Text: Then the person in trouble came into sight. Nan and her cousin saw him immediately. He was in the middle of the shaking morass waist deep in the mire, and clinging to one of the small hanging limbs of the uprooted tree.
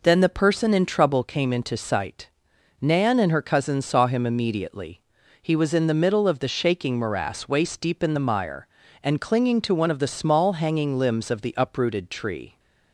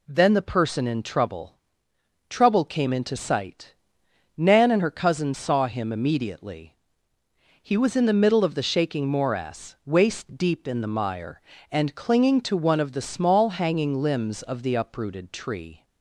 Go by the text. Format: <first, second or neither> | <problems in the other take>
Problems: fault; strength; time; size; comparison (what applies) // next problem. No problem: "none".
first | says "trouble" twice; at 2.2 s